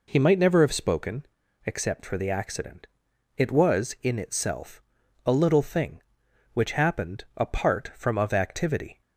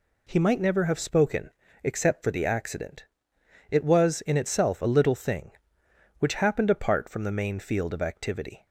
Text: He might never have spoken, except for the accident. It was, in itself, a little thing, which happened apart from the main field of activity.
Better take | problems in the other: second | skips "the main field"; at 8.1 s

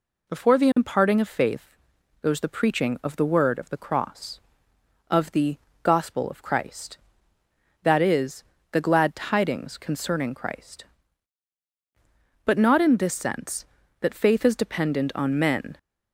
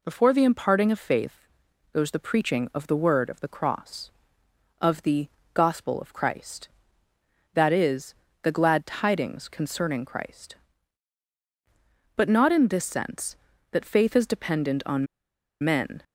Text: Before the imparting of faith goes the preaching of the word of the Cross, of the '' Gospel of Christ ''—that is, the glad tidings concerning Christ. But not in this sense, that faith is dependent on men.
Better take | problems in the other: first | pauses between "faith" and "goes"; noticeable; at 1.4 s; 0.46 s long; noticeable in the first // pauses between "on" and "men"; noticeable; at 15.0 s; 0.56 s long

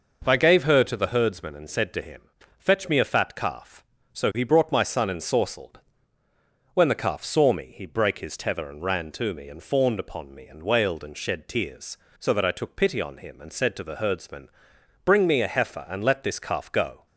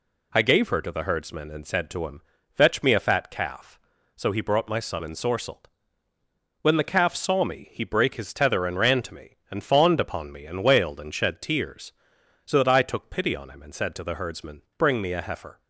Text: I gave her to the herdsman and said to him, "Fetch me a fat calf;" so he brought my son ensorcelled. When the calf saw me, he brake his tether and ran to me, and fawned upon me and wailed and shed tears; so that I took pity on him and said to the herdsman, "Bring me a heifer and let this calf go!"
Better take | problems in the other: first | stops before "and let this calf go"; at 15.5 s

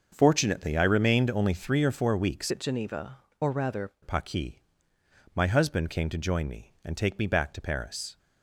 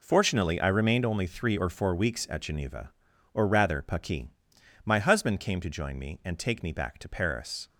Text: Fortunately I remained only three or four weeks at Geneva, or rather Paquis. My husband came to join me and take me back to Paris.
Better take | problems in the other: second | starts louder than the rest; until 1.1 s; 6 dB // changes voice from "at" to "rather"; from 2.4 to 3.9 s; 1.5 s long

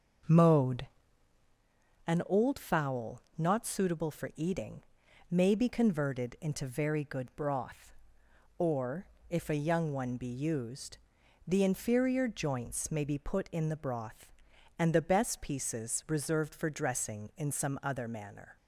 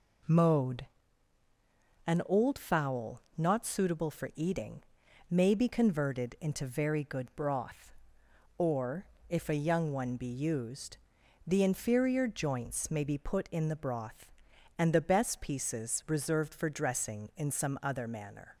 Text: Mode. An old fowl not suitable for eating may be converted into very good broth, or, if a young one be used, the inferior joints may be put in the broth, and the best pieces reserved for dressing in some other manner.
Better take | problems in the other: second | starts louder than the rest; until 1.7 s; 6 dB // pauses between "fowl" and "not"; slight; at 3.2 s; 0.16 s long; slight in the second // pauses between "eating" and "may"; noticeable; at 4.8 s; 0.50 s long; noticeable in the second

